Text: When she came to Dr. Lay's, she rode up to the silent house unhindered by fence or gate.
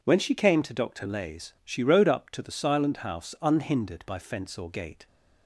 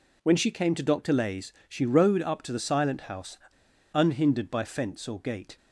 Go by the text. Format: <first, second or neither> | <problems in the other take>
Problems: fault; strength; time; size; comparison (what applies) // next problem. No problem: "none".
first | pauses between "house" and "unhindered"; noticeable; at 3.3 s; 0.57 s long